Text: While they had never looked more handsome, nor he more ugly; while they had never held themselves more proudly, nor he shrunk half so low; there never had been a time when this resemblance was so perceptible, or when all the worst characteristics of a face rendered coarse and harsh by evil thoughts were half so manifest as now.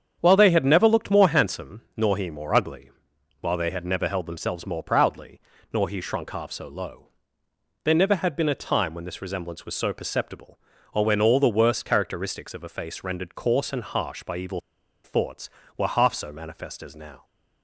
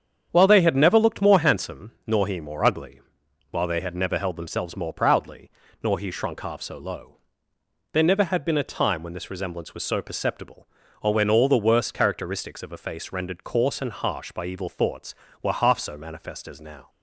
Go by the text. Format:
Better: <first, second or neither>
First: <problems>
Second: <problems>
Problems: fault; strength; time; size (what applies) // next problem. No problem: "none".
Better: second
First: starts louder than the rest; strong; until 1.2 s; 8 dB // pauses between "evil" and "thoughts"; at 14.5 s; 0.45 s long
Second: starts louder than the rest; strong; until 1.3 s; 8 dB